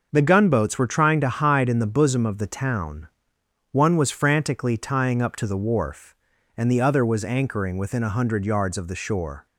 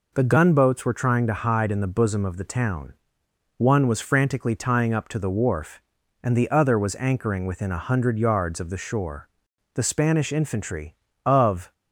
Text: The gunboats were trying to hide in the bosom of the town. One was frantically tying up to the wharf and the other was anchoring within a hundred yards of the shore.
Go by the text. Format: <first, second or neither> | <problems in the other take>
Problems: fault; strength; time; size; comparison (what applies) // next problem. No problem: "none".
first | goes on to say "The Spanish infantry of"; strong; from 9.7 s on; 1.9 s long